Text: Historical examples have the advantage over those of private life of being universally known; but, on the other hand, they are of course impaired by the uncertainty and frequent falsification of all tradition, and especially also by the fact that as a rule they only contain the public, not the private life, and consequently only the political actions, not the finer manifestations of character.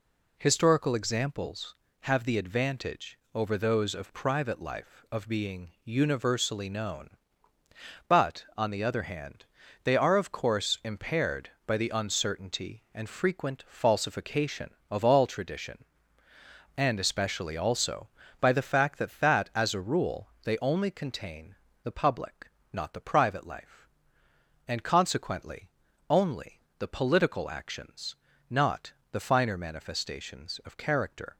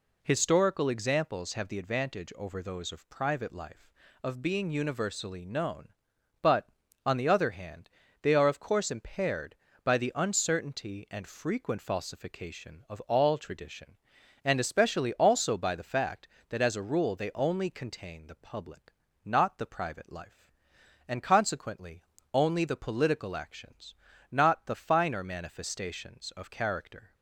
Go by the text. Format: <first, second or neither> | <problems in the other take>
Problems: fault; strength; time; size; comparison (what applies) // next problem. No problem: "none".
second | pauses between "advantage" and "over"; slight; at 3.1 s; 0.16 s long // says "that" twice; at 19.1 s // pauses between "rule" and "they"; slight; at 20.2 s; 0.16 s long // pauses between "contain" and "the"; slight; at 21.5 s; 0.26 s long // pauses between "consequently" and "only"; at 25.6 s; 0.44 s long; slight in the second // pauses between "only" and "the"; slight; at 26.5 s; 0.18 s long // pauses between "not" and "the"; slight; at 28.9 s; 0.20 s long